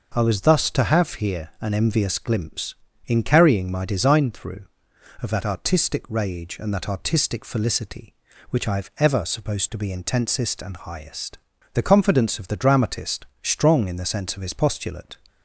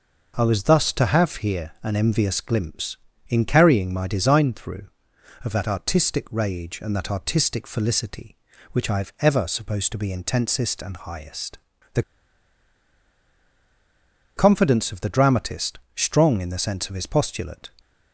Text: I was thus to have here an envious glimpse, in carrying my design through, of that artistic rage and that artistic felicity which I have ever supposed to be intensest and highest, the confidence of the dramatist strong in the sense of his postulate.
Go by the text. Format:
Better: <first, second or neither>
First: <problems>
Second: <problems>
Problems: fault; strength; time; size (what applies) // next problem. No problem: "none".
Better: first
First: pauses between "dramatist" and "strong"; slight; at 13.2 s; 0.18 s long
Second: pauses between "the" and "confidence"; strong; at 12.0 s; 2.3 s long // pauses between "dramatist" and "strong"; slight; at 15.7 s; 0.18 s long